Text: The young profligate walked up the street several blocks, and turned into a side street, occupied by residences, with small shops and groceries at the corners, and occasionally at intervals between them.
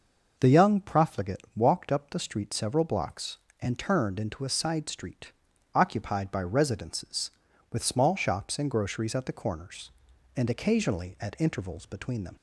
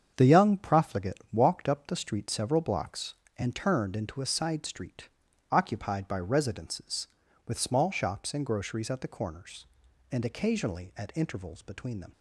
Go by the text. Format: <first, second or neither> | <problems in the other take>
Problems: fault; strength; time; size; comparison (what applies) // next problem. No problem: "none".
first | gets quieter; strong; throughout; 7.5 dB